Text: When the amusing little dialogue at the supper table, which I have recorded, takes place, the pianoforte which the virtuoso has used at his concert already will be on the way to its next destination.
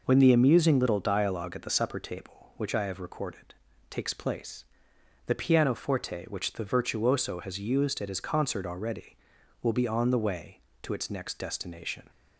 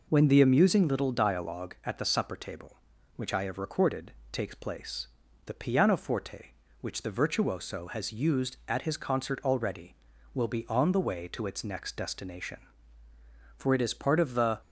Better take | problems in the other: first | goes on to say "For it is part of the"; noticeable; from 13.5 s on; 1.0 s long

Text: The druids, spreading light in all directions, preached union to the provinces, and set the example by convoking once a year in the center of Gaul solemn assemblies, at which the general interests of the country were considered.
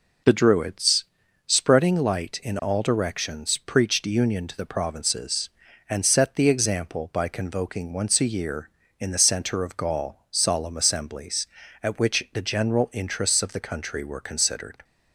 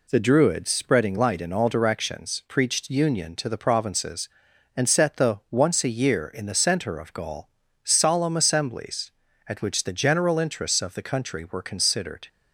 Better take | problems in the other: first | skips "example by convoking"; at 5.4 s // pauses between "Gaul" and "solemn"; slight; at 7.4 s; 0.36 s long

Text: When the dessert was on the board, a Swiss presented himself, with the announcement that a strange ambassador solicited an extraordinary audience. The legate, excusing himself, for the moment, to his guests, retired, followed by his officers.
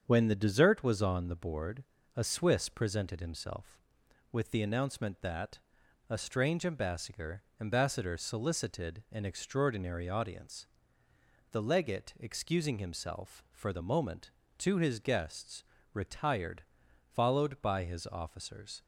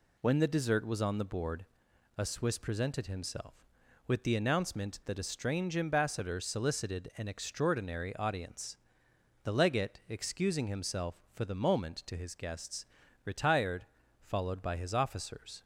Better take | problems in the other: second | starts louder than the rest; strong; until 1.0 s; 7 dB // pauses between "that" and "a"; noticeable; at 5.5 s; 0.50 s long // says "ambassador" twice; at 7.6 s

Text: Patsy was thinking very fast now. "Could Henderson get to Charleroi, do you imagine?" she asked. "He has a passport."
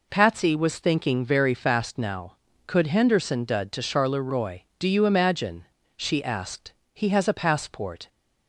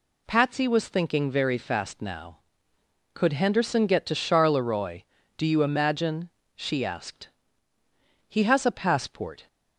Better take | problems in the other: second | says "dud" for "get"; at 3.4 s

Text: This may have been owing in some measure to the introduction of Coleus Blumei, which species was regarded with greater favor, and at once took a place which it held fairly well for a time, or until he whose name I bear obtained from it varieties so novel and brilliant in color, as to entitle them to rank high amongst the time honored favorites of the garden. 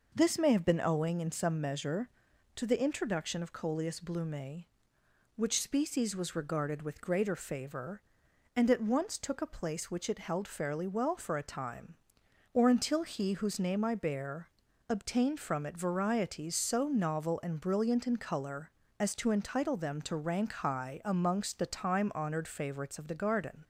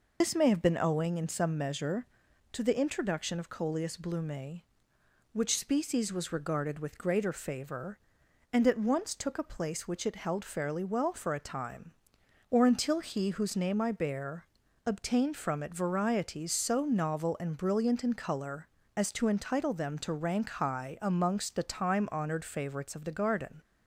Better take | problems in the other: first | loses the start of "This"; at 0.2 s; 110 ms // pauses between "bear" and "obtained"; at 14.4 s; 0.38 s long; also in the first

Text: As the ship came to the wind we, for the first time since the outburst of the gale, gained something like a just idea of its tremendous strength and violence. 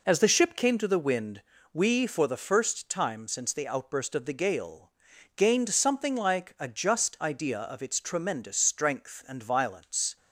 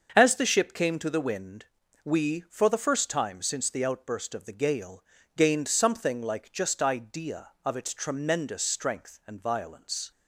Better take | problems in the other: first | starts louder than the rest; until 1.1 s; 6.5 dB // pauses between "wind" and "we"; at 1.6 s; 0.38 s long; slight in the first // skips "a"; at 6.5 s

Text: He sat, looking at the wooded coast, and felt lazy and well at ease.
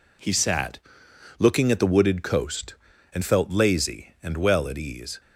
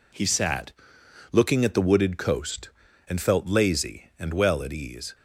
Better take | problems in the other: neither | none

